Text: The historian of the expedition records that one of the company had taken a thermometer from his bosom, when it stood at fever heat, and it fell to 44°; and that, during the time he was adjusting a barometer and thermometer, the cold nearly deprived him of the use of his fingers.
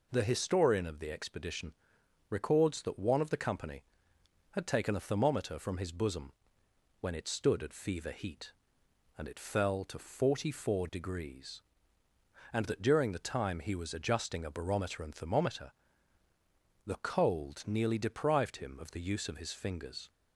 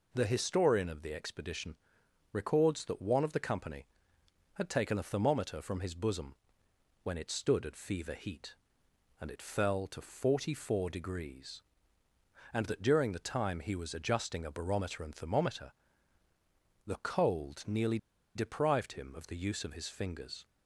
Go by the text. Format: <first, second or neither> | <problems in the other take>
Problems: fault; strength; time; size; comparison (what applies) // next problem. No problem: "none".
first | pauses between "expedition" and "records"; noticeable; at 1.7 s; 0.56 s long; noticeable in the first // pauses between "nearly" and "deprived"; at 17.9 s; 0.37 s long